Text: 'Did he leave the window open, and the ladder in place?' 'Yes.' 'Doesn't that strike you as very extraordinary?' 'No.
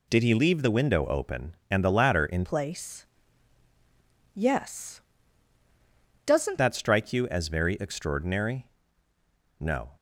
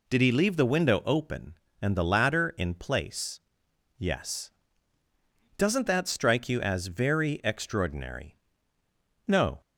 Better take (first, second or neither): second